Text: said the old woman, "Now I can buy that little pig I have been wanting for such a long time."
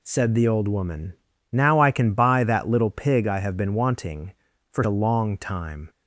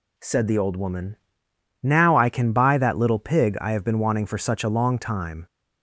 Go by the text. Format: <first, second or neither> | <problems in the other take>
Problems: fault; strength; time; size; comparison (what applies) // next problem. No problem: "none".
second | skips "such"; at 4.8 s